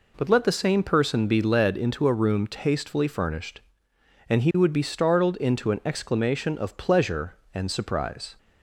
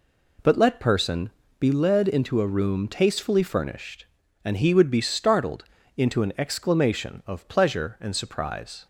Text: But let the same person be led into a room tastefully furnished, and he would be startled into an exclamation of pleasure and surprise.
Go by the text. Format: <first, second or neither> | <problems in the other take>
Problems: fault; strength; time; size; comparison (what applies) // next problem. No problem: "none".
first | skips "the same"; at 0.7 s // pauses between "person" and "be"; slight; at 1.2 s; 0.28 s long // pauses between "startled" and "into"; slight; at 5.6 s; 0.32 s long